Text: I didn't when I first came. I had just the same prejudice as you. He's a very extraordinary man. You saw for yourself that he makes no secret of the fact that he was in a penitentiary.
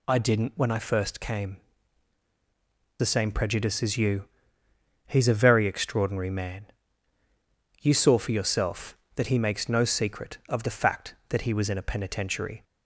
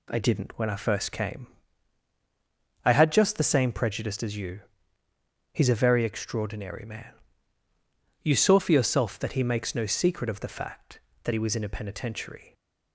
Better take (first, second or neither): second